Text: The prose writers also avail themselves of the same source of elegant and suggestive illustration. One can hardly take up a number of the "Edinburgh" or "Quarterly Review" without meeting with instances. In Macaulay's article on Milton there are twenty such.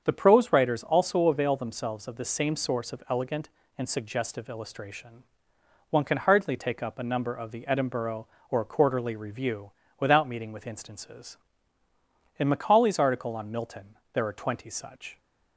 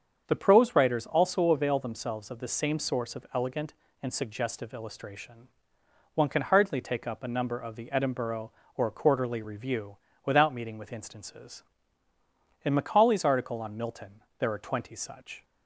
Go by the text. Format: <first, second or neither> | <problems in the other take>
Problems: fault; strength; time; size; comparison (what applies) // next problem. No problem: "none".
neither | starts louder than the rest; the same in both // pauses between "Review" and "without"; slight; the same in both // pauses between "Milton" and "there"; slight; the same in both